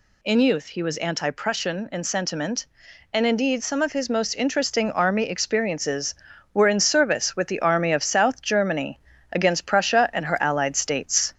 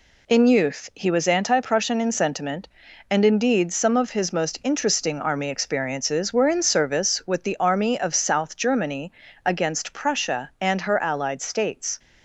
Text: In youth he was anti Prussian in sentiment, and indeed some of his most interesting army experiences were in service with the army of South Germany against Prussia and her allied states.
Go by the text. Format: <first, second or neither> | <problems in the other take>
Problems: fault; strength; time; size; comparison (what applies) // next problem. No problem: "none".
second | gets louder; slight; throughout; 2 dB // pauses between "Germany" and "against"; slight; at 8.9 s; 0.32 s long; slight in the second